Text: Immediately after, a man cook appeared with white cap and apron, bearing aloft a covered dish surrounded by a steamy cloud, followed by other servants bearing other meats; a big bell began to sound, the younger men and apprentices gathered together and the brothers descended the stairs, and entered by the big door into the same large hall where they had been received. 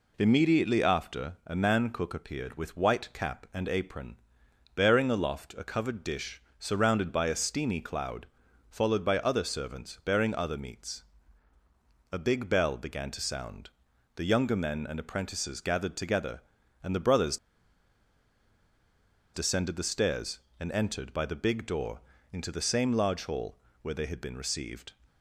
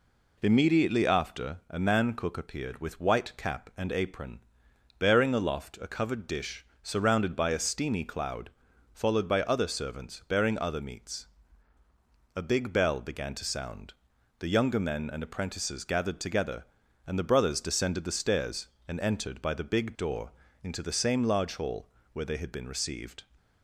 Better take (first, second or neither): second